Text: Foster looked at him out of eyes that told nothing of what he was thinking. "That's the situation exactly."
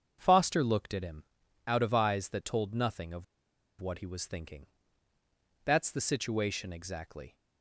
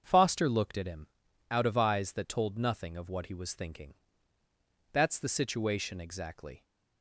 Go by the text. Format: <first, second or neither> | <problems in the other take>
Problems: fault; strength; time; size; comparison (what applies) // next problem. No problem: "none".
second | starts louder than the rest; until 1.2 s; 7 dB; also in the second // pauses between "him" and "out"; at 1.2 s; 0.42 s long; also in the second // pauses between "of" and "what"; noticeable; at 3.2 s; 0.54 s long